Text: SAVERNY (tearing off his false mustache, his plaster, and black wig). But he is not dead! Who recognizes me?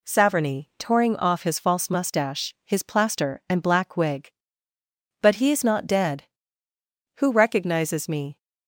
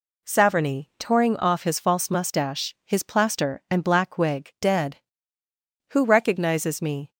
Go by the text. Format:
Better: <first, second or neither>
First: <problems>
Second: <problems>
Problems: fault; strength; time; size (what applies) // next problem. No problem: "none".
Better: first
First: none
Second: skips "But he is not"; at 4.5 s